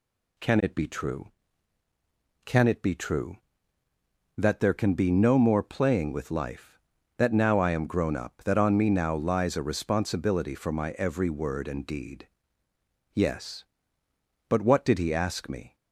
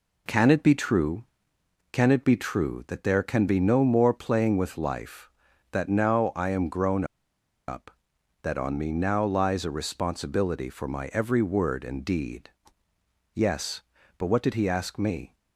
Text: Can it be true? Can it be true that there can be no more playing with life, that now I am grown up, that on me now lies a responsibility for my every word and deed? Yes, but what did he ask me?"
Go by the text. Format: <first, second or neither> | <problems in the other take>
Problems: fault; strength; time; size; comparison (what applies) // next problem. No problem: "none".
first | pauses between "grown" and "up"; noticeable; at 7.0 s; 0.63 s long